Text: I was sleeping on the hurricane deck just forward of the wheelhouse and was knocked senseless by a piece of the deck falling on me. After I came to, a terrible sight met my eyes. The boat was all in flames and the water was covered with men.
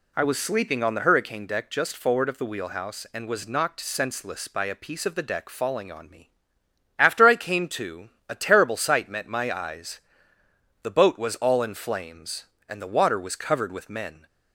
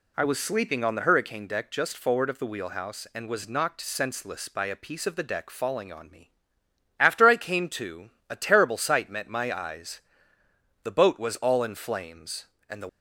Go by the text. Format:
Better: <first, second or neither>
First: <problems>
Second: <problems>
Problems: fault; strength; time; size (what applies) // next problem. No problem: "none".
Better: first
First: none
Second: stops before "water was covered with men"; at 12.8 s